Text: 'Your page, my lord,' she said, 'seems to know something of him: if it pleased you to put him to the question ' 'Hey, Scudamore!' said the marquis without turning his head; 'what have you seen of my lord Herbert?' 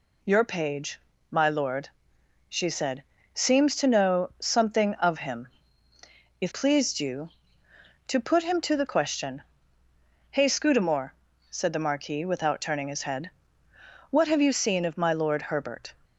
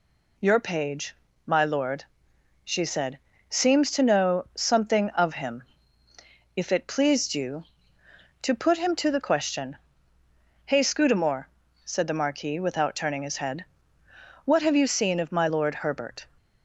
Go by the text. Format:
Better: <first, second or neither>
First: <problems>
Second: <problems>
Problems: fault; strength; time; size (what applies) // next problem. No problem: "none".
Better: second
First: skips "it"; at 6.5 s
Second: none